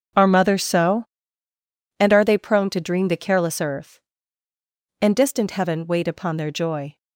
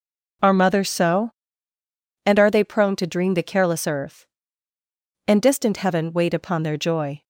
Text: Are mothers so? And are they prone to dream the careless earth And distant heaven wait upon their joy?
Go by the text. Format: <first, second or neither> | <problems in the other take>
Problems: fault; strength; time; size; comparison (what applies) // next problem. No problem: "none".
second | gets quieter; strong; throughout; 12.5 dB